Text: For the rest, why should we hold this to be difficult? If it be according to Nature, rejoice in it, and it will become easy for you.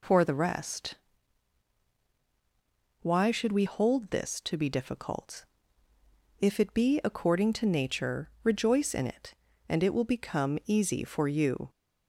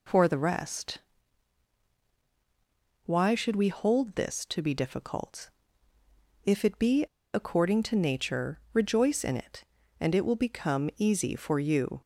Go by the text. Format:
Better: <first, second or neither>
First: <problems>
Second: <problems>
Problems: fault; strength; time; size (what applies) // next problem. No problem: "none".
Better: first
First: none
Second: pauses between "be" and "according"; slight; at 7.0 s; 0.31 s long